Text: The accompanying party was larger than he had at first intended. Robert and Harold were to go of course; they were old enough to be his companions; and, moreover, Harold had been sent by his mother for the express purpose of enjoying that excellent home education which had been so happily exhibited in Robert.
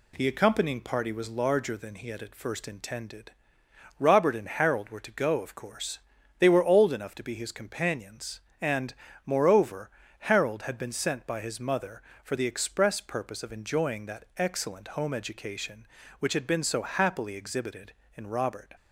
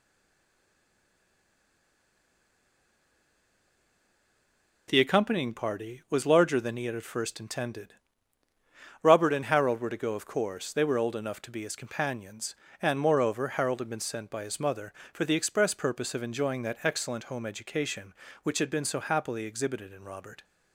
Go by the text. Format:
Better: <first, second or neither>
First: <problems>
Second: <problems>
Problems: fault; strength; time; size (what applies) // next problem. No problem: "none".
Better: first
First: none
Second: stays silent before the first word; strong; until 4.8 s; 4.8 s long